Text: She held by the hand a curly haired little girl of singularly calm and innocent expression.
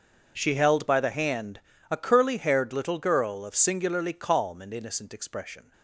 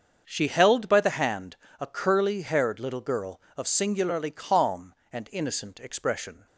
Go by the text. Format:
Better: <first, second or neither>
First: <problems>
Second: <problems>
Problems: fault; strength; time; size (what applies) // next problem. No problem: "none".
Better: neither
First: starts louder than the rest; until 1.3 s; 6.5 dB // pauses between "hand" and "a"; slight; at 1.6 s; 0.30 s long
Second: starts louder than the rest; until 1.2 s; 7 dB // pauses between "hand" and "a"; slight; at 1.5 s; 0.24 s long